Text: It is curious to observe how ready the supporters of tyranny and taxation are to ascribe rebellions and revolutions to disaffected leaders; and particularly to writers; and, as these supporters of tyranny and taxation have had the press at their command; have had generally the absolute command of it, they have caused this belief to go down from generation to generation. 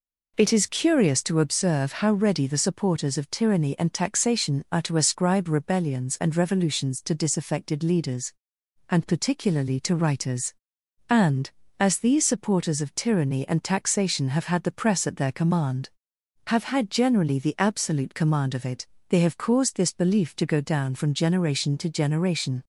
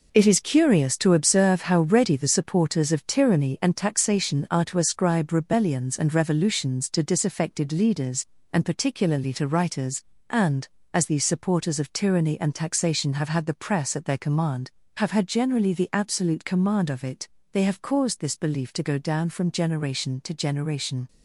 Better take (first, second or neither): first